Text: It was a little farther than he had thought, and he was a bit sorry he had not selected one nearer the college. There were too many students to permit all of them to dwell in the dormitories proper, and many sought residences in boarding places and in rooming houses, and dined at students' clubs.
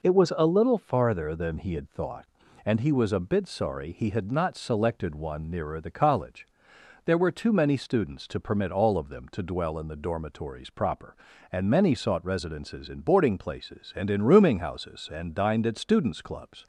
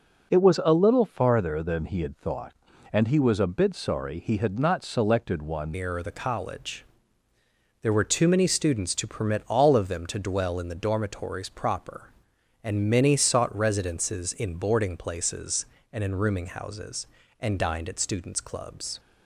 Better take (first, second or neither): first